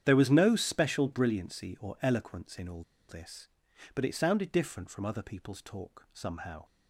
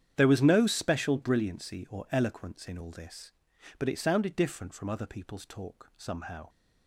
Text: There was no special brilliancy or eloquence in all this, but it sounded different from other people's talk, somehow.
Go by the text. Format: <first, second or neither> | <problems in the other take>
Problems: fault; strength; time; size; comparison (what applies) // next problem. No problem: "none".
second | starts louder than the rest; strong; until 1.0 s; 9.5 dB; strong in the second // pauses between "all" and "this"; slight; at 2.8 s; 0.26 s long